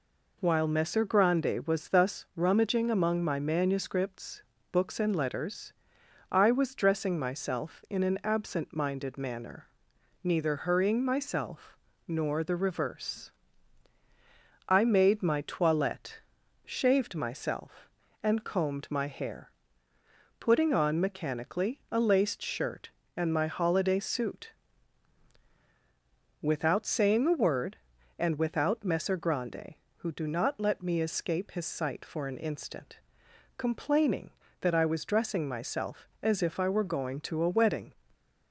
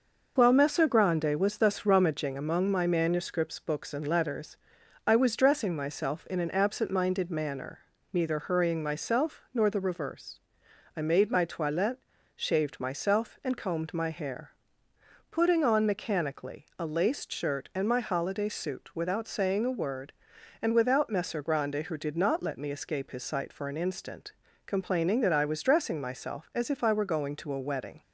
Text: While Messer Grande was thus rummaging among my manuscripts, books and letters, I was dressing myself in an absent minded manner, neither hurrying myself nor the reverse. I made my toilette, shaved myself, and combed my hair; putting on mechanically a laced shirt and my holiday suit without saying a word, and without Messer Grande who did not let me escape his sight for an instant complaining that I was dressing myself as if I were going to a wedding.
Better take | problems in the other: second | pauses between "myself" and "nor"; slight; at 11.7 s; 0.30 s long // pauses between "suit" and "without"; strong; at 24.4 s; 1.9 s long // says "do" for "did"; at 30.1 s // pauses between "instant" and "complaining"; noticeable; at 32.9 s; 0.58 s long; slight in the second // stays silent after the last word; slight; from 37.9 s on; 0.6 s long

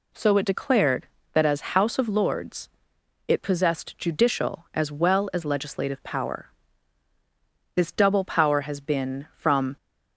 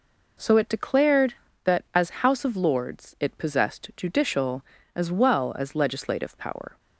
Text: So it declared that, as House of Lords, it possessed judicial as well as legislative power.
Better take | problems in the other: second | goes on to say "This double power has been from"; strong; from 7.7 s on; 2.0 s long

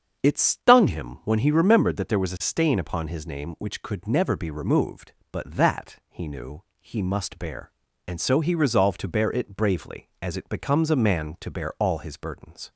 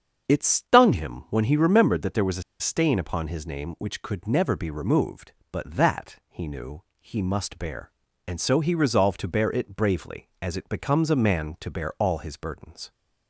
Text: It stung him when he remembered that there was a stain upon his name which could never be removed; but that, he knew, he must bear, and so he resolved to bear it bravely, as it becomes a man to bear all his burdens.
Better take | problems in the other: first | starts louder than the rest; strong; until 1.3 s; 7.5 dB; strong in the first // pauses between "a" and "stain"; slight; at 2.4 s; 0.17 s long

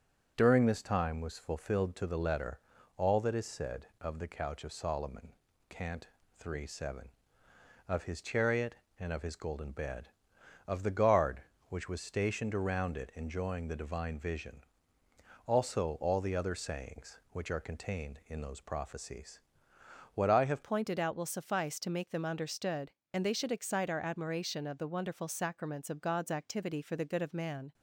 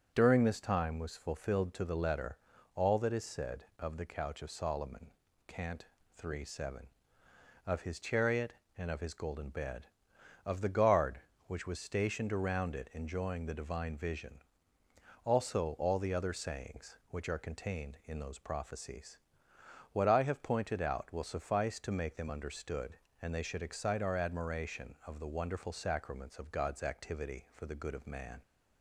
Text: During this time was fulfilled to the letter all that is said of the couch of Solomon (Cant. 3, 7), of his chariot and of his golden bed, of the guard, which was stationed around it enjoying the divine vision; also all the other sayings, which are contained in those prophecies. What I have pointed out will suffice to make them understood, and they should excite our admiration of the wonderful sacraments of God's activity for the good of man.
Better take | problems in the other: second | pauses between "letter" and "all"; at 2.5 s; 0.38 s long; also in the second // changes voice at "pointed"; from 20.6 s on; 7.1 s long

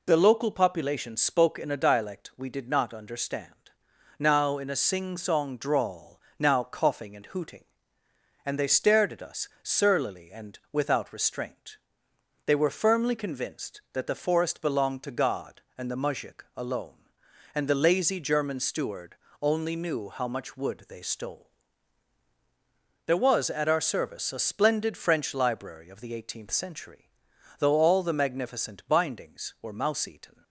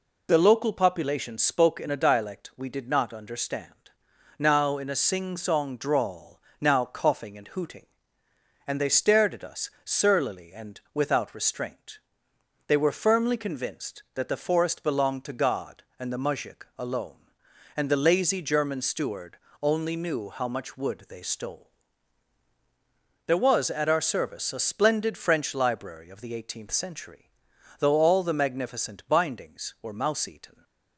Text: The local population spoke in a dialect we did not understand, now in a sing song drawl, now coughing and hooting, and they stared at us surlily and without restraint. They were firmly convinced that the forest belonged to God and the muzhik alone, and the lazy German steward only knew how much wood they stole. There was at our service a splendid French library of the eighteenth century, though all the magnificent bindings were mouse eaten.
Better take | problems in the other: neither | pauses between "us" and "surlily"; slight; the same in both // pauses between "steward" and "only"; slight; the same in both

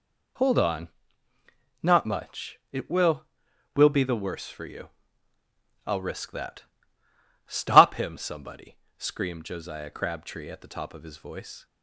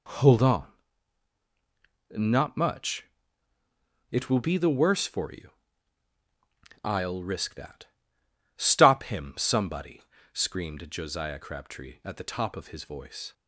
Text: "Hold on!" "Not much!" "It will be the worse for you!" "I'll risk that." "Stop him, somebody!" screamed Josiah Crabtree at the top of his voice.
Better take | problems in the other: second | says "will" twice; at 3.7 s

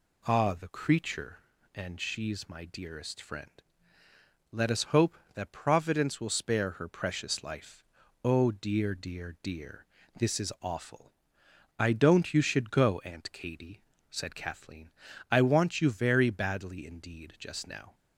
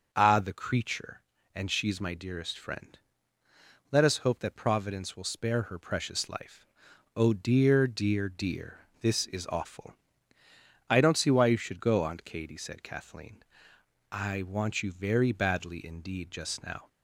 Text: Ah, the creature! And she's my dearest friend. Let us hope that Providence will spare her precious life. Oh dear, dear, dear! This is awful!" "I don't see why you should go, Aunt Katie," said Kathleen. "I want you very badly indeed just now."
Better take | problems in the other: second | skips "see why"; at 12.3 s

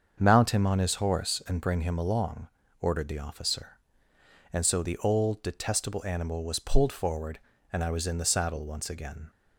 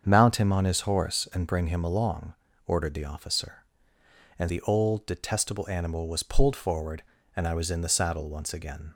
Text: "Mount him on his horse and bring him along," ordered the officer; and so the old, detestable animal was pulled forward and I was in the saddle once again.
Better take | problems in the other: first | starts louder than the rest; strong; until 1.0 s; 7.5 dB; also in the first // skips "so"; at 4.4 s

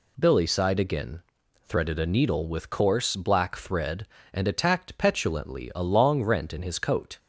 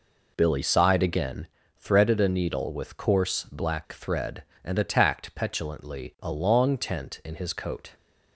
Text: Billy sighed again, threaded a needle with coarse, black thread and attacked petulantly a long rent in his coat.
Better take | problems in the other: first | says "tent" for "rent"; at 6.7 s

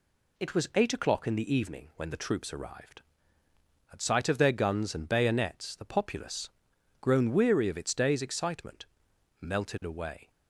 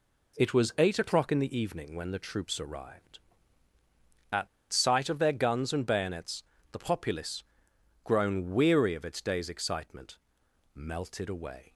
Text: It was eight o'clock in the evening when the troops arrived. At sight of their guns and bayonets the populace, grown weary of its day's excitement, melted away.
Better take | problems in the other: first | pauses between "At" and "sight"; slight; at 4.4 s; 0.25 s long // pauses between "bayonets" and "the"; slight; at 6.4 s; 0.30 s long

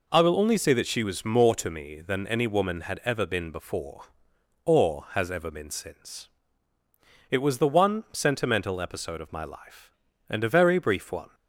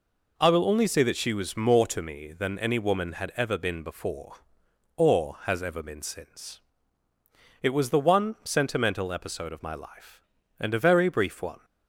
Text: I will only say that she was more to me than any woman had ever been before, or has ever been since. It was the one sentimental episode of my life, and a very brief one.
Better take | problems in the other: neither | none

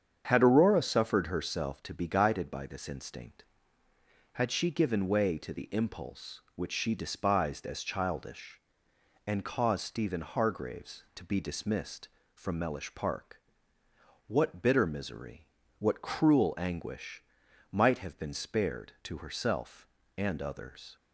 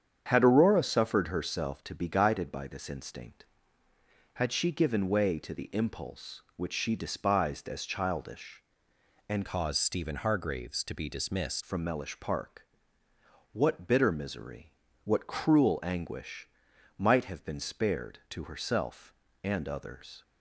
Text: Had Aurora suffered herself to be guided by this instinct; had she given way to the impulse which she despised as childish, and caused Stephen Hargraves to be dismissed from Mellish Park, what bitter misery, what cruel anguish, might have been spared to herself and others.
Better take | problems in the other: first | starts louder than the rest; strong; until 1.2 s; 8 dB; strong in the first // changes voice from "caused" to "dismissed"; from 9.4 to 11.6 s; 2.2 s long

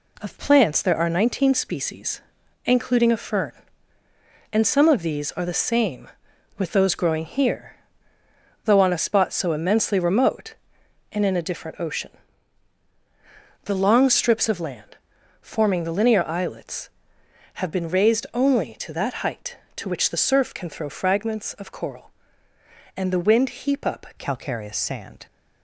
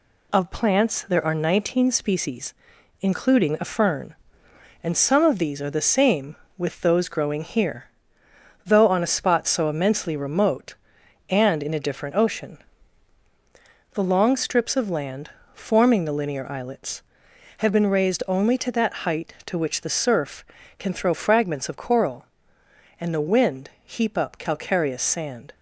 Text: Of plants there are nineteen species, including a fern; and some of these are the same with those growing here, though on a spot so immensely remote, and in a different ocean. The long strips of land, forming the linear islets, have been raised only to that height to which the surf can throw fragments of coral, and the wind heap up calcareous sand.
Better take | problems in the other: second | changes voice at "calcareous"; from 24.1 s on; 1.1 s long

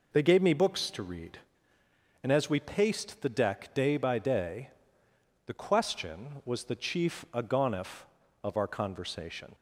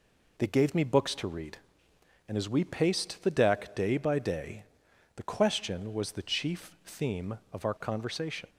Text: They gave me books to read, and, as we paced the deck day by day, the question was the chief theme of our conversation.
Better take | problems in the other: second | says "agonif" for "theme"; at 7.3 s

